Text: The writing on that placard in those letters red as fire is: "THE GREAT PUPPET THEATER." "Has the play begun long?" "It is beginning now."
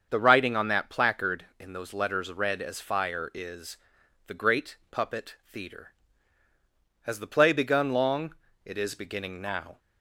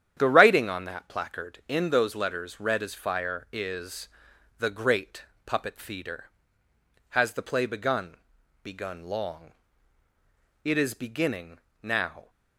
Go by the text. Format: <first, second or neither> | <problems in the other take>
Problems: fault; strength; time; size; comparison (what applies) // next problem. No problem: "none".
first | starts louder than the rest; strong; until 1.1 s; 9.5 dB; also in the first // pauses between "GREAT" and "PUPPET"; slight; at 5.2 s; 0.24 s long // says "begun" twice; at 8.6 s // pauses between "beginning" and "now"; slight; at 11.5 s; 0.24 s long